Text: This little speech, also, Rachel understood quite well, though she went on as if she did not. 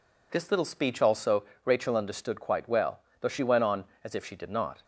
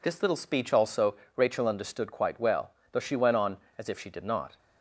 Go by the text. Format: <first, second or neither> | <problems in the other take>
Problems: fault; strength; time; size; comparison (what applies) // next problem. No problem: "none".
neither | none